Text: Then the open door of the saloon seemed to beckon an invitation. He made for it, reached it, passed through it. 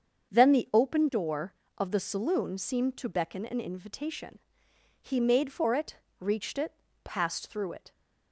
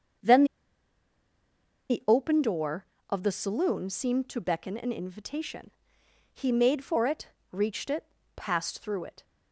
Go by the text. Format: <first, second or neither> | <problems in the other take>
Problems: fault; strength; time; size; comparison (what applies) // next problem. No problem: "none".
first | starts louder than the rest; until 2.7 s; 7 dB; also in the first // pauses between "Then" and "the"; strong; at 0.4 s; 1.4 s long